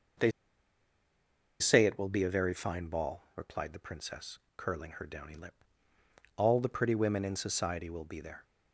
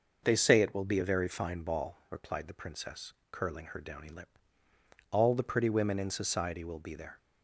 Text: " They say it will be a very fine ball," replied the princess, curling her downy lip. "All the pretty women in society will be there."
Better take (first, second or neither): second